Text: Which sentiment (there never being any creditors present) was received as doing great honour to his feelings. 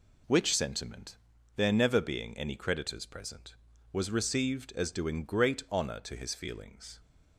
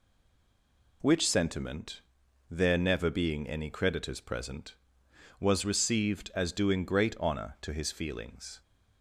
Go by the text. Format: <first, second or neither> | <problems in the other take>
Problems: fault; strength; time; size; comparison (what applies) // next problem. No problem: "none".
first | stays silent before the first word; until 1.0 s; 1.0 s long